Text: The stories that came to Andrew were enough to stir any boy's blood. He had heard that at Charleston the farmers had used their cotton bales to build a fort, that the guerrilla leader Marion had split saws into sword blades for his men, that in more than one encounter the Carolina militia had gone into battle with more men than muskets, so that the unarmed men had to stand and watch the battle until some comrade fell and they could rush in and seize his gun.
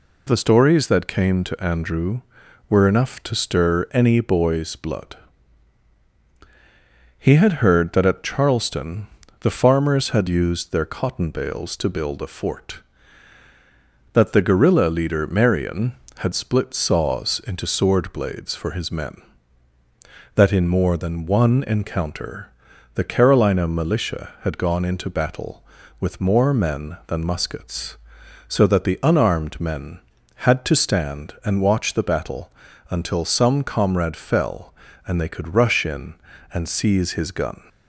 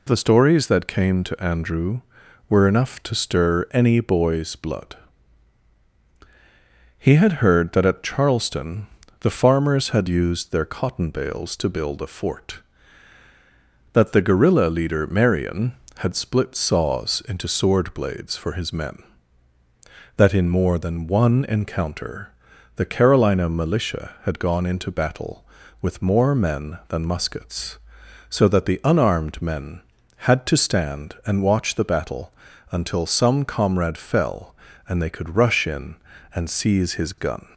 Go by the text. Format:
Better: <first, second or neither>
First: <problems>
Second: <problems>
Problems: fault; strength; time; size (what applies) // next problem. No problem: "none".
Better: neither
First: pauses between "Charleston" and "the"; slight; at 9.0 s; 0.34 s long // pauses between "encounter" and "the"; at 22.5 s; 0.44 s long // pauses between "battle" and "until"; at 32.5 s; 0.40 s long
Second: pauses between "Charleston" and "the"; slight; at 8.8 s; 0.34 s long // pauses between "encounter" and "the"; at 22.3 s; 0.44 s long // pauses between "battle" and "until"; at 32.3 s; 0.40 s long